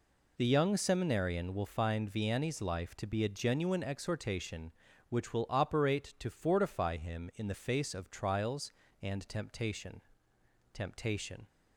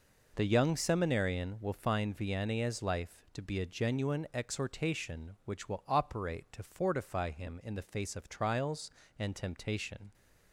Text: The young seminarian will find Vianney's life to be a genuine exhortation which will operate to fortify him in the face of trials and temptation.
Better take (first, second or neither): second